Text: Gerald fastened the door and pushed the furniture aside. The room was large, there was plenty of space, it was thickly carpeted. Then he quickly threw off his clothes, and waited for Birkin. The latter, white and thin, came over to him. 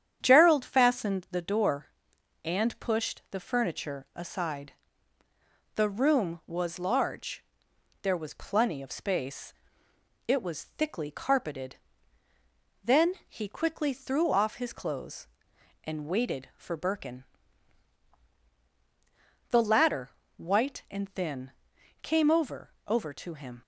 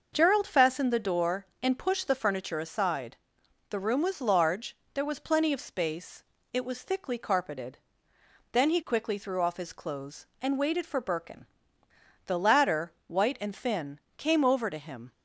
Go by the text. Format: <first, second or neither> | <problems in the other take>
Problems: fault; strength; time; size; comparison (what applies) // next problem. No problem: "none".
second | starts louder than the rest; strong; until 1.2 s; 8.5 dB; noticeable in the second // says "over" twice; at 22.8 s